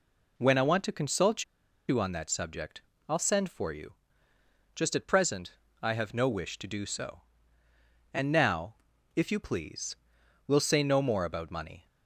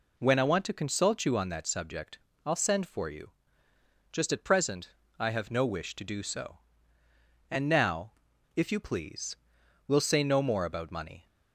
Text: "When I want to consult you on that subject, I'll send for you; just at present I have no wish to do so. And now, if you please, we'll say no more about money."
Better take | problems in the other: second | pauses between "consult" and "you"; at 1.4 s; 0.44 s long // pauses between "present" and "I"; slight; at 5.5 s; 0.30 s long; slight in the second

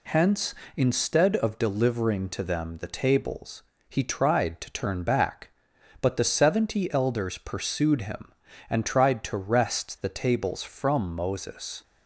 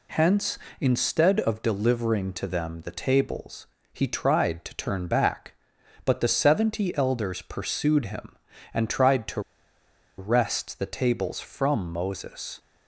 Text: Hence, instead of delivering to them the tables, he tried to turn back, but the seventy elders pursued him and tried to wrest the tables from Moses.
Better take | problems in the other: first | pauses between "to" and "wrest"; noticeable; at 9.4 s; 0.77 s long

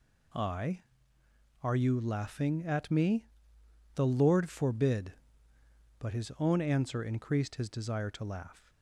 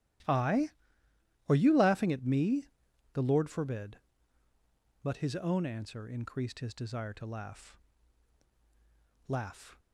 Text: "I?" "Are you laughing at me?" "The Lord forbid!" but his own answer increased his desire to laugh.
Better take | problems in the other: first | starts louder than the rest; strong; until 2.0 s; 14 dB // says "laugh" twice; at 9.2 s

